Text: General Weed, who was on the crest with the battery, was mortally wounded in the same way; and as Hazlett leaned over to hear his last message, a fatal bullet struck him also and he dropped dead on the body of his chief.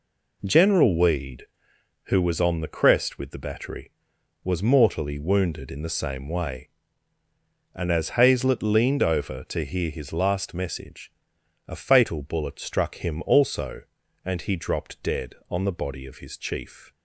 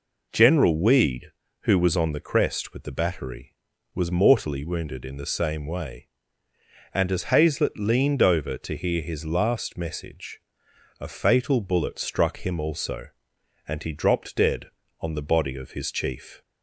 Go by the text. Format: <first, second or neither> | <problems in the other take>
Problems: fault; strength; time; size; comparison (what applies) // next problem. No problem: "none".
neither | none